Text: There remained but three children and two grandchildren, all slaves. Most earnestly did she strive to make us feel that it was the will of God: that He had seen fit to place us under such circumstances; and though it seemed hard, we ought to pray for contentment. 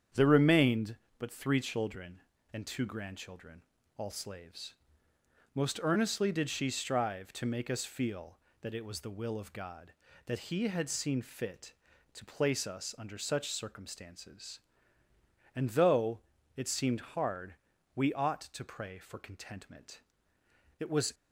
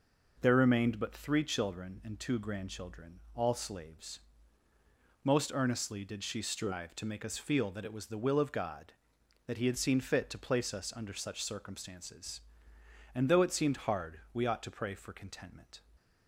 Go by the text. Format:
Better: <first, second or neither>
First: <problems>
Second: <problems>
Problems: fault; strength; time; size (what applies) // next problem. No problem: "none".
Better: second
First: starts louder than the rest; strong; until 1.3 s; 8 dB // pauses between "though" and "it"; at 16.1 s; 0.38 s long // goes on to say "It was"; slight; from 20.7 s on; 0.36 s long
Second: none